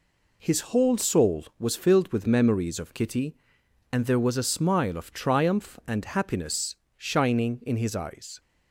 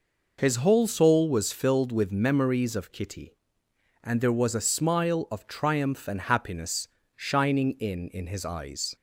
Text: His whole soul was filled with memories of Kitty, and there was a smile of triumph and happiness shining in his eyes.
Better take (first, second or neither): first